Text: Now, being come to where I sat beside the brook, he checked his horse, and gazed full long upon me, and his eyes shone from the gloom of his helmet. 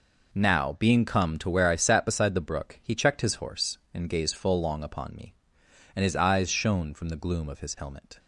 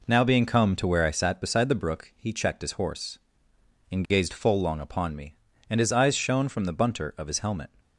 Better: first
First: none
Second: says "bunter" for "gloom"; at 6.7 s

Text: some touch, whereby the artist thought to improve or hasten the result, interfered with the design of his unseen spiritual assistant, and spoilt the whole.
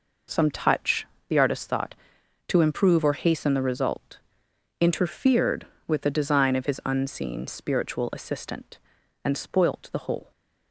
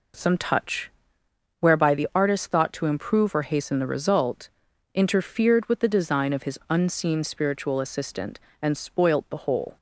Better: second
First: skips "whereby"; at 1.1 s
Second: none

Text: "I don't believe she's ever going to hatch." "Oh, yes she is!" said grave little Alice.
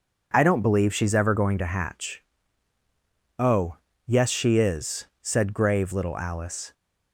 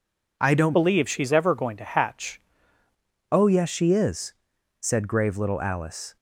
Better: first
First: none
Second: changes voice from "believe" to "hatch"; from 0.7 to 2.3 s; 1.6 s long

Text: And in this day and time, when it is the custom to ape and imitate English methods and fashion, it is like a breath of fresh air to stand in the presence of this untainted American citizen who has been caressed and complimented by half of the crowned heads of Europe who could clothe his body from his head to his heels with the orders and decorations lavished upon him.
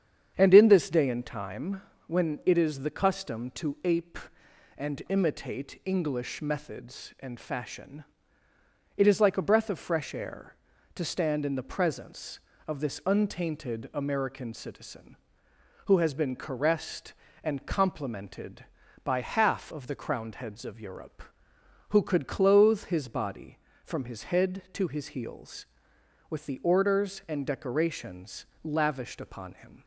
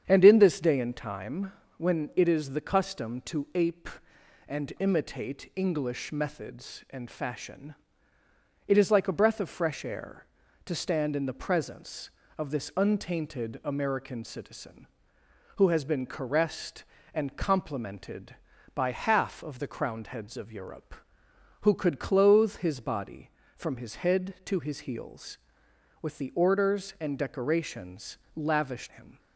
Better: first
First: starts louder than the rest; strong; until 1.3 s; 8 dB // pauses between "decorations" and "lavished"; slight; at 28.4 s; 0.16 s long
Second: starts louder than the rest; strong; until 1.0 s; 8 dB // pauses between "decorations" and "lavished"; slight; at 28.1 s; 0.16 s long // skips "upon"; at 28.8 s

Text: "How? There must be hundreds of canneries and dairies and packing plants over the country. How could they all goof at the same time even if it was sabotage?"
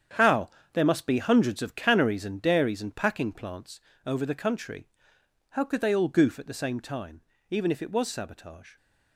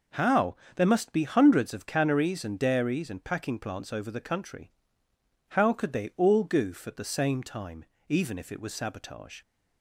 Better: second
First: gets quieter; strong; throughout; 10.5 dB // pauses between "plants" and "over"; slight; at 3.7 s; 0.26 s long // pauses between "time" and "even"; slight; at 7.2 s; 0.26 s long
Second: pauses between "time" and "even"; slight; at 7.8 s; 0.24 s long

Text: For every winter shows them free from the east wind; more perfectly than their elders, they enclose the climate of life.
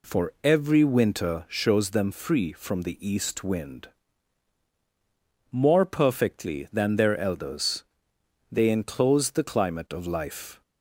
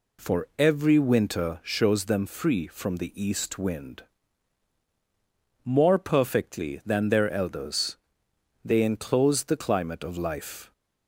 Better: neither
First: none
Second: none

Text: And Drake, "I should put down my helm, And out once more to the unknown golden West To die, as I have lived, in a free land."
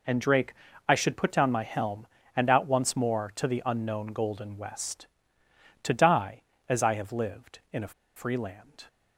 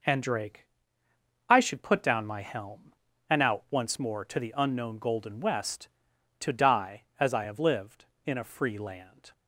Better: second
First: pauses between "a" and "free"; slight; at 7.9 s; 0.23 s long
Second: none

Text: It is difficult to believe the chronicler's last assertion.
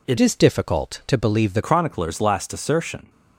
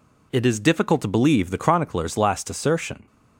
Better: second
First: changes voice from "is" to "the"; from 0.1 to 1.6 s; 1.5 s long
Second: none

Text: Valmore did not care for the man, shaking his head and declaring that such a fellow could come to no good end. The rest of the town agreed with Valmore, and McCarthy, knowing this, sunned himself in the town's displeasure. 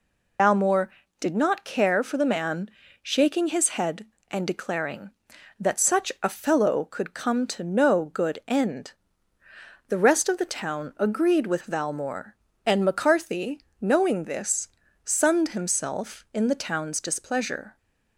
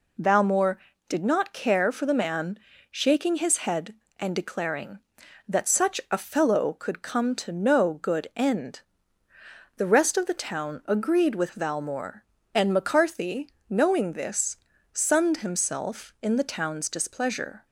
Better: second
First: loses the start of "Valmore"; at 0.3 s; 100 ms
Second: none

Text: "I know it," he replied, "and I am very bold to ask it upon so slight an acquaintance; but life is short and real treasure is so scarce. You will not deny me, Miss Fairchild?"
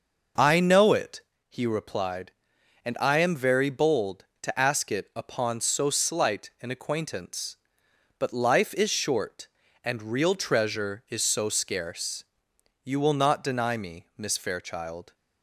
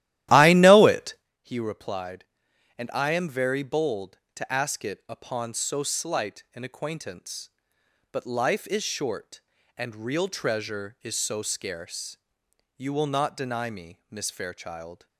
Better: first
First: none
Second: starts louder than the rest; strong; until 1.3 s; 14 dB

